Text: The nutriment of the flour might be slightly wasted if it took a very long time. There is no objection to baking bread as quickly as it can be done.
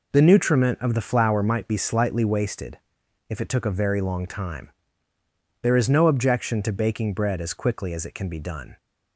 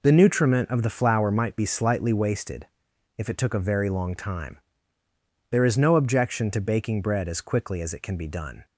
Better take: neither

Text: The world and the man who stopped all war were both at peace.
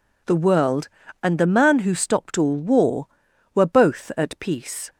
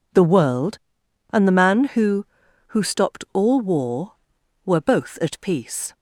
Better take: first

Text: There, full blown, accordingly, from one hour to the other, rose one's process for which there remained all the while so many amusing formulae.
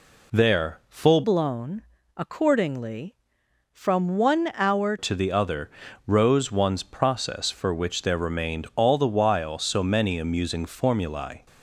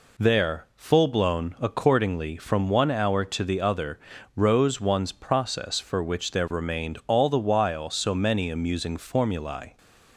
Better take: second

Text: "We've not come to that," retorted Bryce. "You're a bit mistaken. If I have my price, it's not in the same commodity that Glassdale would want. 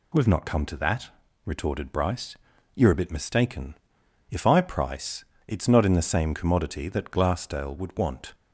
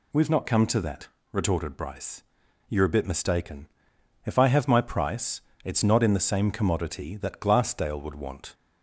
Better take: second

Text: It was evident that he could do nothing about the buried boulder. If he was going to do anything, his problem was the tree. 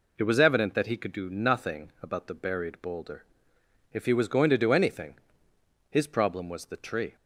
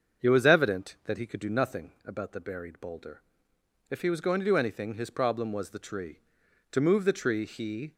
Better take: first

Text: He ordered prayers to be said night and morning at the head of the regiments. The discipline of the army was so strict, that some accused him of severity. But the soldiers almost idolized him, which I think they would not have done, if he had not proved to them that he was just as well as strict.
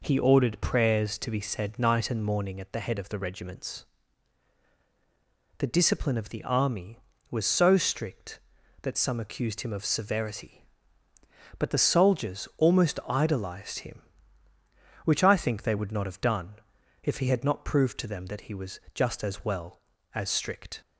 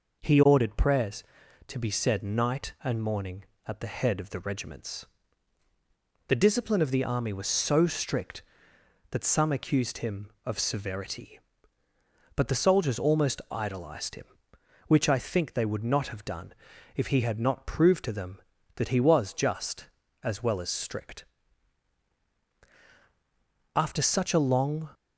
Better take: first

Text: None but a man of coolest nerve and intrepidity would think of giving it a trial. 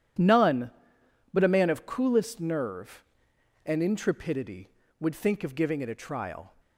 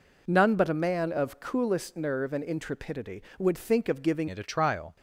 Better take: first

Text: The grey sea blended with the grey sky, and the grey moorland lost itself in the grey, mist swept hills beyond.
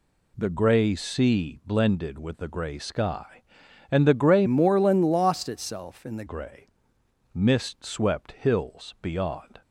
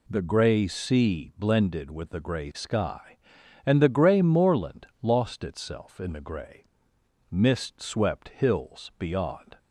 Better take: second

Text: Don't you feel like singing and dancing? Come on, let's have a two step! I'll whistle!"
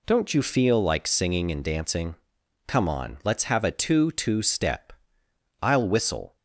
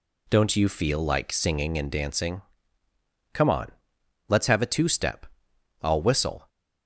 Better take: second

